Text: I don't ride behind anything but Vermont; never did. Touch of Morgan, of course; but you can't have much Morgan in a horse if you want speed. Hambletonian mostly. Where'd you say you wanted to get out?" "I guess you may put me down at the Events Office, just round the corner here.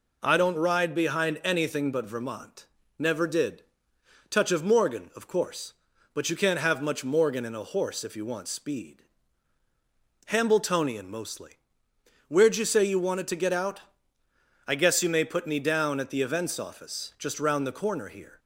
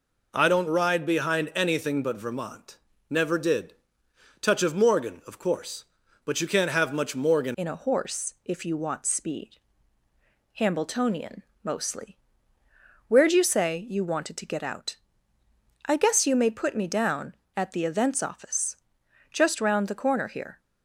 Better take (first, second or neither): first